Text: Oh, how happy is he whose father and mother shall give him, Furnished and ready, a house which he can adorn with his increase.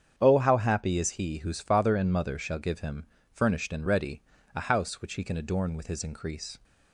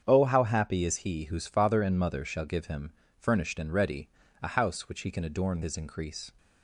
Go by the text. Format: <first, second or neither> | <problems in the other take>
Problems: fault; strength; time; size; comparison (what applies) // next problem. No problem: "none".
first | starts louder than the rest; strong; until 1.0 s; 7.5 dB; strong in the first // skips "with"; at 5.6 s